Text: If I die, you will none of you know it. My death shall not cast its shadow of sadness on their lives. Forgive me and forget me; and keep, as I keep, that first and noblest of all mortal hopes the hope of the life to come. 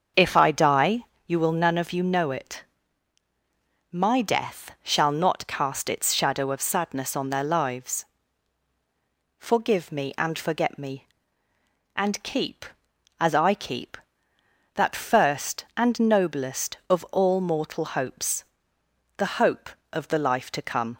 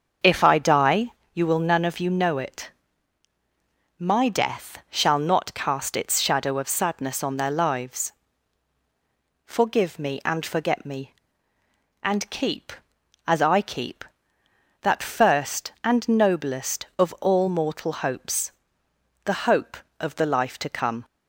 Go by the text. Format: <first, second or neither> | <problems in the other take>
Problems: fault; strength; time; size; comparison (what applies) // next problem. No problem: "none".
neither | starts louder than the rest; the same in both // pauses between "hopes" and "the"; noticeable; the same in both